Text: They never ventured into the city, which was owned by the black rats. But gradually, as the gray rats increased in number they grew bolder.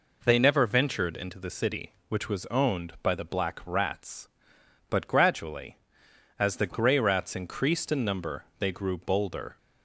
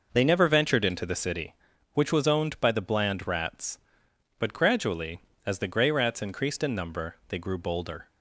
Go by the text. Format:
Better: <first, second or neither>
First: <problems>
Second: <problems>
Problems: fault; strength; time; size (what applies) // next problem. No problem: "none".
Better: first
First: none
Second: says "bland" for "black"; at 2.8 s